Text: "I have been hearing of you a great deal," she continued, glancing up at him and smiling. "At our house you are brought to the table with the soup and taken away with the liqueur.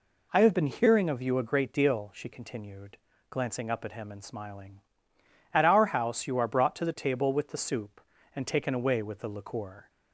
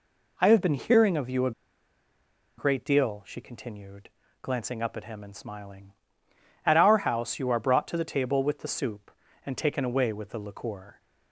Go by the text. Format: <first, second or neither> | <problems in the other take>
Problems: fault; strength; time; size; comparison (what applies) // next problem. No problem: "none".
first | pauses between "a" and "great"; at 1.5 s; 1.0 s long